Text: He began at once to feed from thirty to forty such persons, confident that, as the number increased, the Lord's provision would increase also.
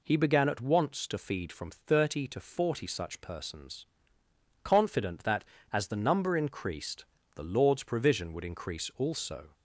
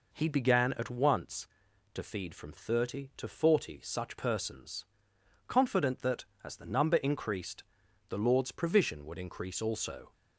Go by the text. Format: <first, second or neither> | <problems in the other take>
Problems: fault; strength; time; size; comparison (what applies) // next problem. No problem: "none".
neither | none